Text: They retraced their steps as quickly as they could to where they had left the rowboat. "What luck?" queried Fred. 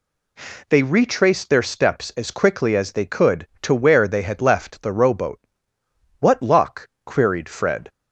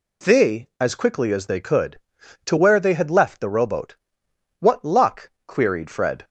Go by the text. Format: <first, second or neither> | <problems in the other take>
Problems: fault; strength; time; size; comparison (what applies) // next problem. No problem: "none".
first | skips "retraced their steps"; at 0.7 s